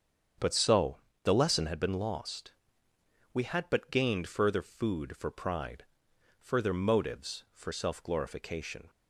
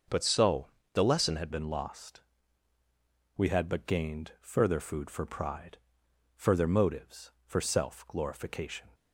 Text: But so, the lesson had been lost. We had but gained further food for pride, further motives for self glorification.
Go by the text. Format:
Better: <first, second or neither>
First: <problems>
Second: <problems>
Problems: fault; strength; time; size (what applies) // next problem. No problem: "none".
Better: first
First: starts louder than the rest; strong; until 1.6 s; 7.5 dB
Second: starts louder than the rest; until 1.3 s; 6 dB // changes voice at "been"; from 1.5 s on; 7.4 s long